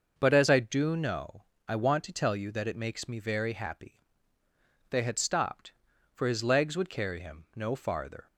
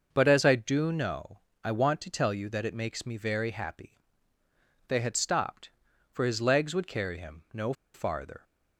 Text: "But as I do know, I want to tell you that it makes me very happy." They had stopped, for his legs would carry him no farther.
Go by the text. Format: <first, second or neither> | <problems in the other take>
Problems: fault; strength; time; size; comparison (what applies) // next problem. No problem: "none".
first | starts louder than the rest; noticeable; until 1.1 s; 6 dB; also in the first // pauses between "no" and "farther"; slight; at 7.7 s; 0.21 s long